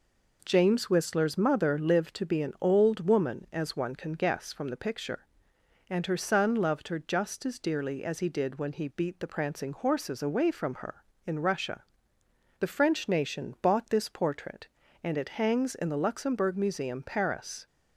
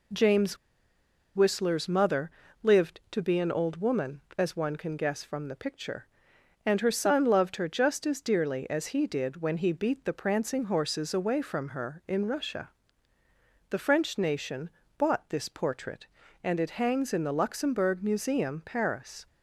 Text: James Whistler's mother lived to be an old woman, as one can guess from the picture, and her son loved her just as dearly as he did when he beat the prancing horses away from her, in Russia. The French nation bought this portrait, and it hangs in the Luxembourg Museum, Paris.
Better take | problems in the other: first | pauses between "James" and "Whistler's"; noticeable; at 0.5 s; 0.79 s long // pauses between "mother" and "lived"; slight; at 2.2 s; 0.32 s long // pauses between "nation" and "bought"; slight; at 14.6 s; 0.30 s long

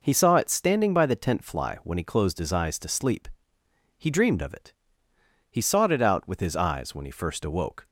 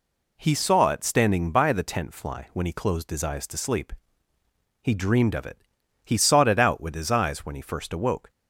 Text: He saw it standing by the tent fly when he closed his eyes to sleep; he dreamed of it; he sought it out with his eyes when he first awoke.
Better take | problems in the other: neither | none

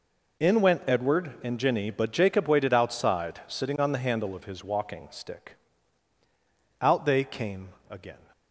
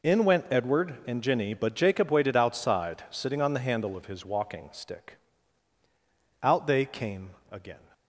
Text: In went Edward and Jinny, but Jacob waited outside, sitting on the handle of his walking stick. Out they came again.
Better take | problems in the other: neither | pauses between "came" and "again"; slight; the same in both

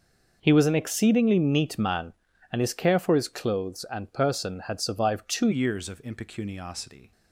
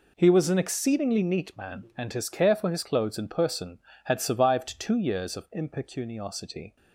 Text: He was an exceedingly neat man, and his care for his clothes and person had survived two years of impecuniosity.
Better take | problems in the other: second | changes voice at "years"; from 5.5 s on; 1.6 s long

